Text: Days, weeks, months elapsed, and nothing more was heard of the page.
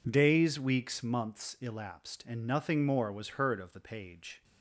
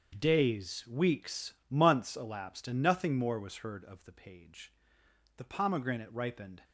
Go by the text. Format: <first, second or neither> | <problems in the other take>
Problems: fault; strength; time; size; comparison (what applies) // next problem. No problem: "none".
first | starts louder than the rest; until 1.2 s; 7 dB // goes on to say "The pomegranate ripened"; noticeable; from 5.3 s on; 1.2 s long